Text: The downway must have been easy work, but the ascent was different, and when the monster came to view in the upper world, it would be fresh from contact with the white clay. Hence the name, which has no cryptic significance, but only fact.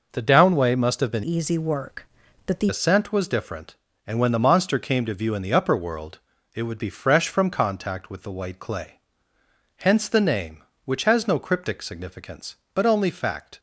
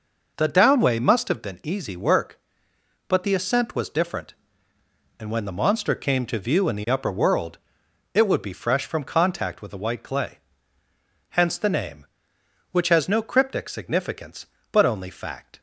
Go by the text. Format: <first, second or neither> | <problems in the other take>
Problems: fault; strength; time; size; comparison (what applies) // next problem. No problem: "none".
second | changes voice from "easy" to "the"; from 1.2 to 2.6 s; 1.4 s long